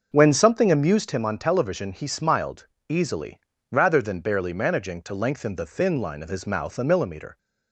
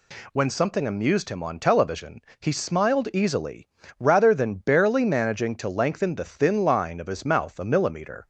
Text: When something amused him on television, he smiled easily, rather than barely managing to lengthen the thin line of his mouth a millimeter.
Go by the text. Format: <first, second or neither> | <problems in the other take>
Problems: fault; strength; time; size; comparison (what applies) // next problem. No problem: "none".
second | starts louder than the rest; noticeable; until 1.1 s; 6 dB // pauses between "smiled" and "easily"; slight; at 2.6 s; 0.24 s long